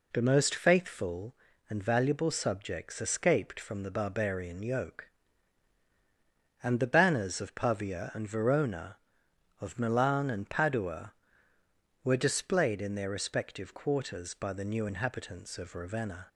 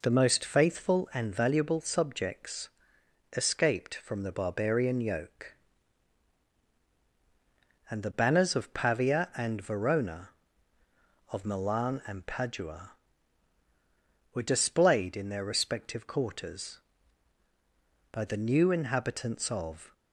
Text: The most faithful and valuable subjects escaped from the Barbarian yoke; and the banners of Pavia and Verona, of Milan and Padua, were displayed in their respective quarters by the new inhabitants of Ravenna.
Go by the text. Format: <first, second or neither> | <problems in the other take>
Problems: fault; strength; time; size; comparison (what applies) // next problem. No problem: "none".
first | pauses between "subjects" and "escaped"; noticeable; at 2.6 s; 0.64 s long // stops before "Ravenna"; at 19.9 s